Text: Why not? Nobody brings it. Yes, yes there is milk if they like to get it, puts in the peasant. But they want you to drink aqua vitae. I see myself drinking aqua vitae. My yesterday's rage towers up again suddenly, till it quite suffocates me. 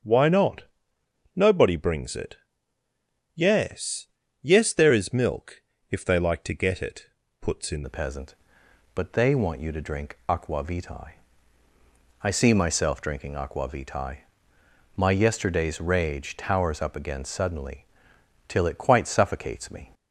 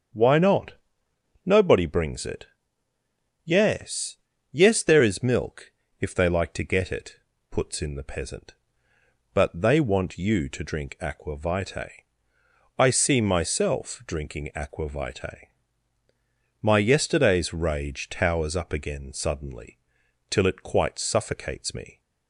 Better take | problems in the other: second | starts louder than the rest; strong; until 1.7 s; 7.5 dB; strong in the second // pauses between "milk" and "if"; slight; at 5.6 s; 0.28 s long; slight in the second // changes voice at "the"; from 7.8 s on; 12.1 s long

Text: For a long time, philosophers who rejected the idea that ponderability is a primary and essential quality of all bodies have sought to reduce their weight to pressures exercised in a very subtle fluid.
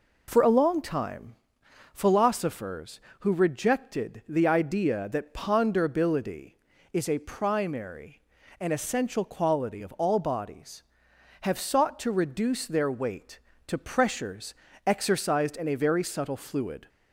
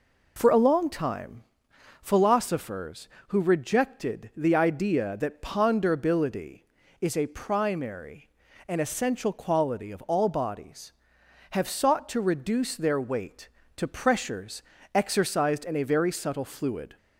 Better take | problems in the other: neither | pauses between "pressures" and "exercised"; slight; the same in both

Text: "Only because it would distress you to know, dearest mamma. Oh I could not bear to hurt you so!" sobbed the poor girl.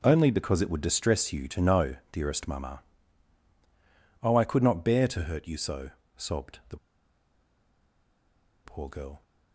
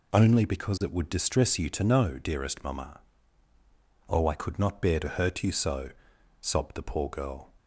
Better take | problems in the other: second | pauses between "the" and "poor"; strong; at 6.7 s; 1.8 s long

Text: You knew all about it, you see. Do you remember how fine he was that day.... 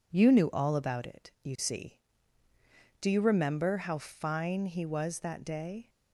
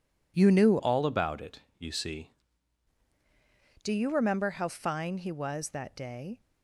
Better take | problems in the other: first | changes voice from "all" to "see"; from 0.7 to 2.3 s; 1.6 s long

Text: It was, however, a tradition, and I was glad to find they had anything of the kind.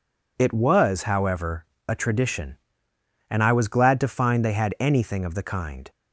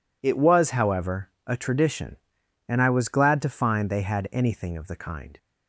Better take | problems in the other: neither | none

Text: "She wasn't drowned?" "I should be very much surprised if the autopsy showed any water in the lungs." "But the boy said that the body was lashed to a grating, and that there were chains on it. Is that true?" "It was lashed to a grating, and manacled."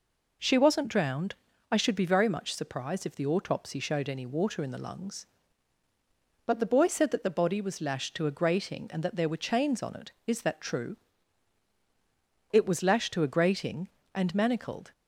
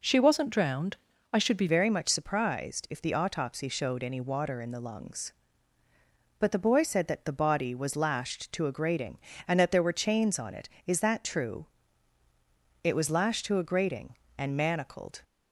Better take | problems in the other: first | changes voice at "very"; from 1.6 s on; 13.6 s long

